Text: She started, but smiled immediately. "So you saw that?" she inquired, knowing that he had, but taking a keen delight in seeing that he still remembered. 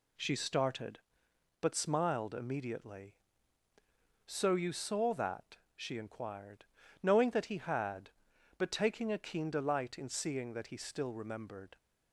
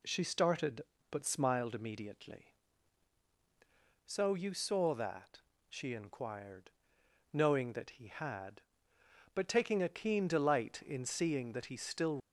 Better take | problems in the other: first | stops before "remembered"; at 12.1 s

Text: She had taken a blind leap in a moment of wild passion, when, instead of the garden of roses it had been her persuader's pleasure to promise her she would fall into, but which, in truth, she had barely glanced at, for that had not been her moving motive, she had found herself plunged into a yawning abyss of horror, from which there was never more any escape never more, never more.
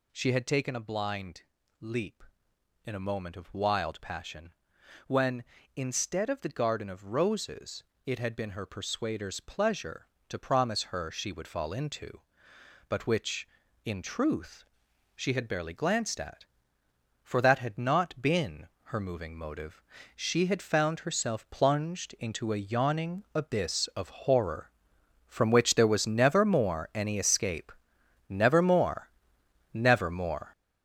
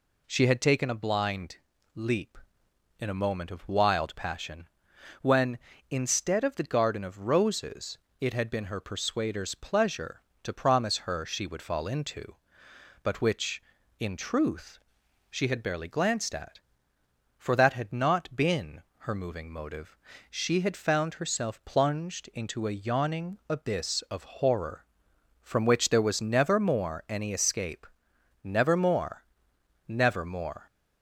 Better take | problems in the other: second | gets louder; strong; throughout; 8 dB // pauses between "blind" and "leap"; at 1.4 s; 0.38 s long; also in the second // pauses between "roses" and "it"; slight; at 7.8 s; 0.22 s long; slight in the second // pauses between "been" and "her"; slight; at 18.6 s; 0.18 s long; slight in the second // pauses between "escape" and "never"; noticeable; at 27.7 s; 0.60 s long; noticeable in the second

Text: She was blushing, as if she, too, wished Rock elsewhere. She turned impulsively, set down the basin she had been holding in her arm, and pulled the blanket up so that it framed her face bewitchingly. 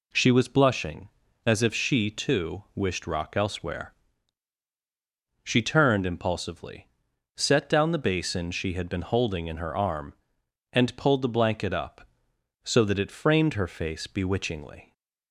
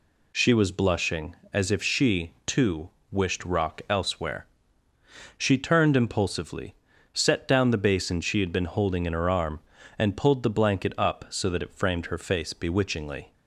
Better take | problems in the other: neither | none

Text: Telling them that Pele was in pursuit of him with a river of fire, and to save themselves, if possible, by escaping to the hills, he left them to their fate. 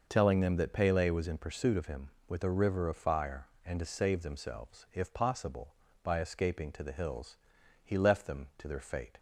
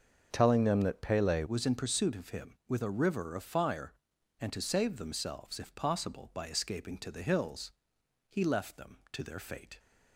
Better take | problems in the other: first | starts louder than the rest; until 1.3 s; 6.5 dB // changes voice at "was"; from 1.4 s on; 8.3 s long

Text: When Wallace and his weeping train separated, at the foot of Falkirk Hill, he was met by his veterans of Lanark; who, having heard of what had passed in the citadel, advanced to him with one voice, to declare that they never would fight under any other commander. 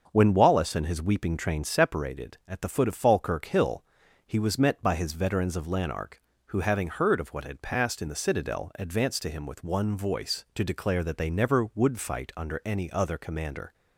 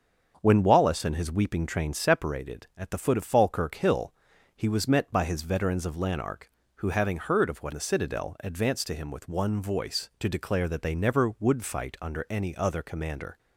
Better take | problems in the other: first | starts louder than the rest; until 1.4 s; 7 dB; also in the first // skips "had passed in"; at 7.7 s

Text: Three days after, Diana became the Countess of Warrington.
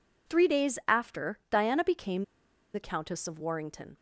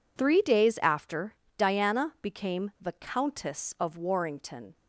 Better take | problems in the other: second | pauses between "became" and "the"; noticeable; at 2.2 s; 0.49 s long

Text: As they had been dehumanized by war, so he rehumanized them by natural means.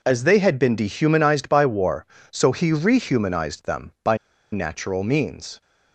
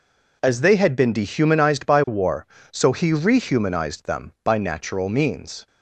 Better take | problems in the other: second | pauses between "by" and "natural"; slight; at 4.1 s; 0.35 s long

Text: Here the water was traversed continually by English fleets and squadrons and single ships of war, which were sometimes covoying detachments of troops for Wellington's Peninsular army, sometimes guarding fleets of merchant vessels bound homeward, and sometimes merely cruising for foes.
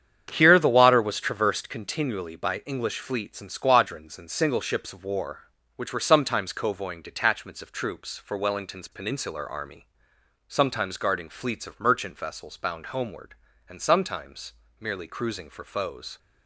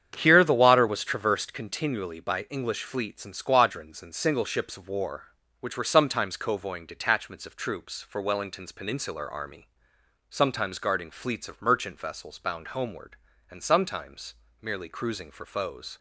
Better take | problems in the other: neither | starts louder than the rest; strong; the same in both // pauses between "sometimes" and "merely"; slight; the same in both

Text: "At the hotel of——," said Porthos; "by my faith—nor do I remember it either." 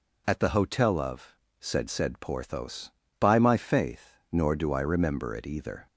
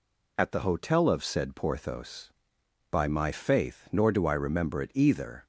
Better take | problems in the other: second | says "said" twice; at 1.9 s

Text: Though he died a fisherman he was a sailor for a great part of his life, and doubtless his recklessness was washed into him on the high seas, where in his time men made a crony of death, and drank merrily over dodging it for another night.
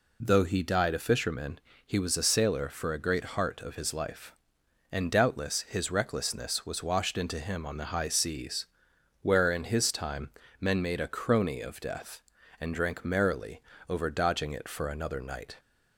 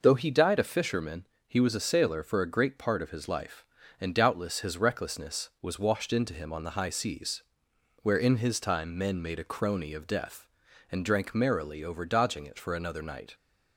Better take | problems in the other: second | pauses between "fisherman" and "he"; slight; at 1.5 s; 0.28 s long; slight in the second // says "heart" for "part"; at 3.2 s // pauses between "time" and "men"; slight; at 10.2 s; 0.30 s long // pauses between "merrily" and "over"; slight; at 13.6 s; 0.28 s long

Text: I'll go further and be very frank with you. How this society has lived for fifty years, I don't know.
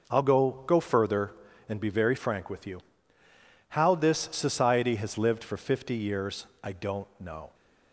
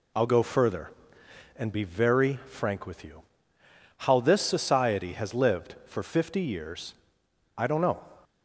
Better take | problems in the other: second | says "go" twice; at 0.6 s

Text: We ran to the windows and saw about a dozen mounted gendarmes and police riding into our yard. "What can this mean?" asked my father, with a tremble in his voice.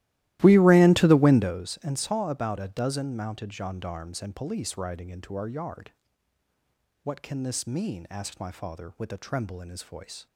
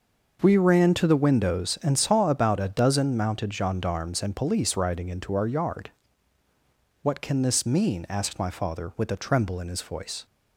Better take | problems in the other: second | starts louder than the rest; strong; until 1.5 s; 16 dB

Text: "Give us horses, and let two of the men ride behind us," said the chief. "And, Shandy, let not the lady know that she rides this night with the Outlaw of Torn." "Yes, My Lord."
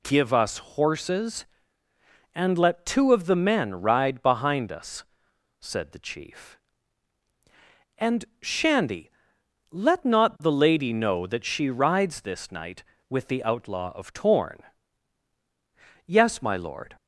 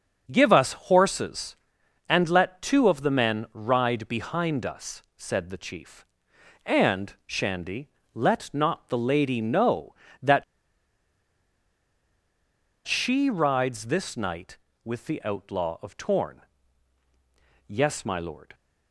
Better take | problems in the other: first | starts louder than the rest; until 1.3 s; 7 dB // pauses between "that" and "she"; strong; at 10.4 s; 2.4 s long

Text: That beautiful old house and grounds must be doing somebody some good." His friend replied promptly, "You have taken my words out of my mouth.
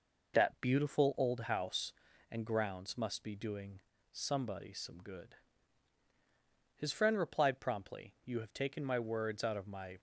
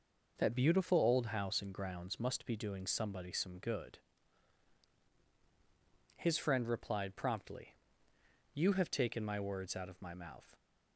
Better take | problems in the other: second | pauses between "doing" and "somebody"; slight; at 3.7 s; 0.32 s long // stops before "mouth"; at 9.9 s

